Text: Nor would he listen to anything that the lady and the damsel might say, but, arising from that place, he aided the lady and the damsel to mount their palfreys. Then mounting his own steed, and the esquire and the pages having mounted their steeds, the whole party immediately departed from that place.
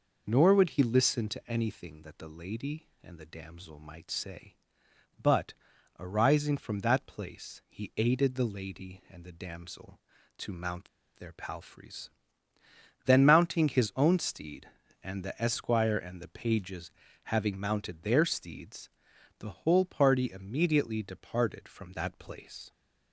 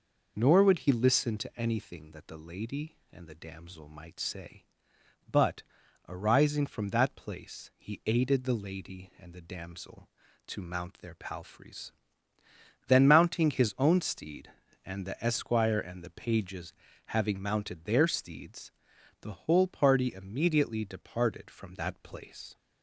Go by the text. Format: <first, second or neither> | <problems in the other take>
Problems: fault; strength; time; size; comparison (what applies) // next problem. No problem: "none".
second | pauses between "mount" and "their"; slight; at 10.8 s; 0.29 s long // pauses between "pages" and "having"; slight; at 16.9 s; 0.32 s long; slight in the second